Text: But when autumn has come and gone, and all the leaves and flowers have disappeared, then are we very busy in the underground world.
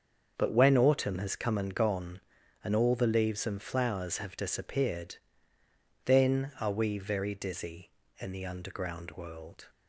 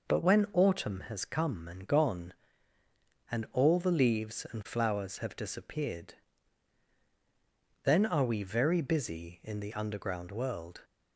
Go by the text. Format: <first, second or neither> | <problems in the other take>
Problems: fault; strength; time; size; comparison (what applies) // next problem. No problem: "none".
second | starts louder than the rest; until 1.3 s; 7 dB // says "dizzy" for "busy"; at 7.3 s